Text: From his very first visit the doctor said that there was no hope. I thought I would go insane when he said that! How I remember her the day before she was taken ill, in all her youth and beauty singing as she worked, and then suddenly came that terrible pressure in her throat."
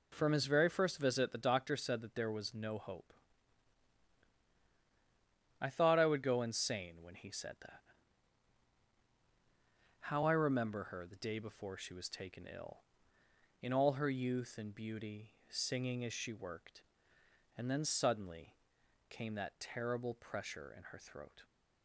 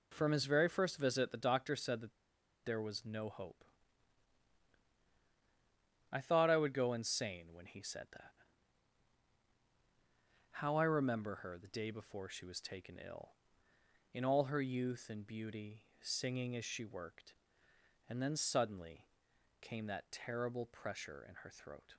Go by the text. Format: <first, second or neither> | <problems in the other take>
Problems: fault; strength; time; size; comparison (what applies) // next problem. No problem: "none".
first | pauses between "that" and "there"; noticeable; at 2.1 s; 0.51 s long // pauses between "beauty" and "singing"; slight; at 15.8 s; 0.16 s long; slight in the first // pauses between "suddenly" and "came"; noticeable; at 19.0 s; 0.52 s long; noticeable in the first